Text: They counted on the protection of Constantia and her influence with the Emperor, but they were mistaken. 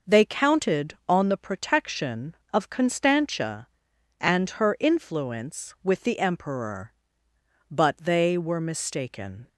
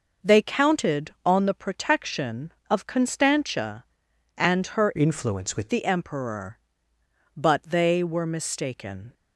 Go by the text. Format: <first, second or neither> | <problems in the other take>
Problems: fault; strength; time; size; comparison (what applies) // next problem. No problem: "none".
first | changes voice from "influence" to "with"; from 4.9 to 5.7 s; 0.8 s long